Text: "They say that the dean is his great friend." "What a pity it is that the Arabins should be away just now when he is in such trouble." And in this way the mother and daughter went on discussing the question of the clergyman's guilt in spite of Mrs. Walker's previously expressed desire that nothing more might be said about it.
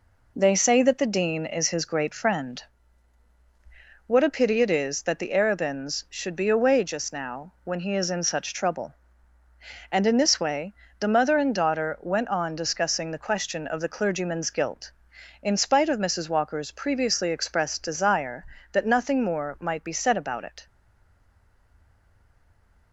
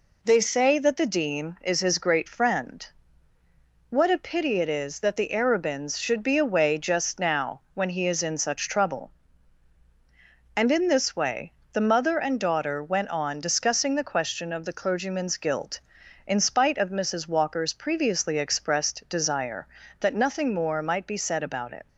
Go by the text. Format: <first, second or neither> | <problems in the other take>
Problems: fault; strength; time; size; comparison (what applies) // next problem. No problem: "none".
second | pauses between "way" and "the"; slight; at 10.7 s; 0.24 s long; slight in the second // stays silent after the last word; from 20.6 s on; 2.3 s long